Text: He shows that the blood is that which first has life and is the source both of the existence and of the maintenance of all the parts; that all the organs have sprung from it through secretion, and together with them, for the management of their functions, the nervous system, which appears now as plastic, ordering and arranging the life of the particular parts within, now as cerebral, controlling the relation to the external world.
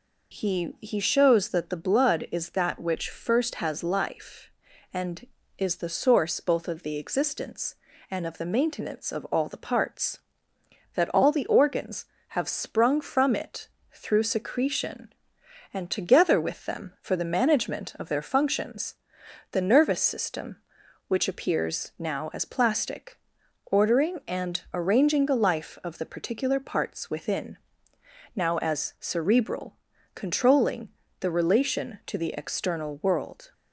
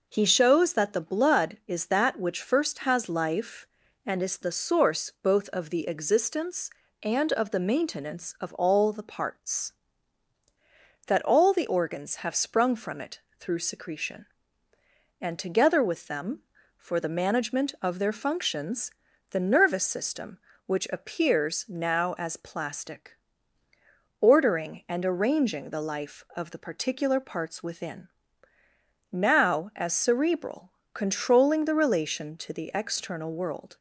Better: second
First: says "He" twice; at 0.8 s // pauses between "it" and "through"; slight; at 13.6 s; 0.24 s long // pauses between "controlling" and "the"; slight; at 30.9 s; 0.30 s long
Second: pauses between "it" and "through"; slight; at 13.1 s; 0.18 s long

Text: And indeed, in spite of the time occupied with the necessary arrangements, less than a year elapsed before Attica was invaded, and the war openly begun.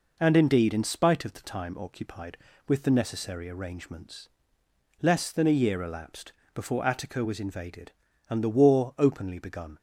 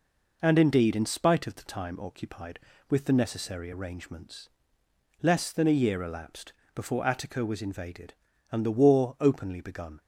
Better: neither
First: pauses between "elapsed" and "before"; slight; at 6.3 s; 0.22 s long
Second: pauses between "elapsed" and "before"; slight; at 6.5 s; 0.22 s long

